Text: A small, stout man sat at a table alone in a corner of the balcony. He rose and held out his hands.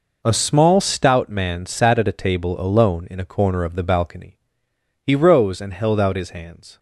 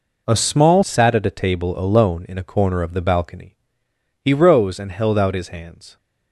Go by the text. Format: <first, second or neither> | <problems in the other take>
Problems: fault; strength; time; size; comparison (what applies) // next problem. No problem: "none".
first | skips "stout man"; at 0.8 s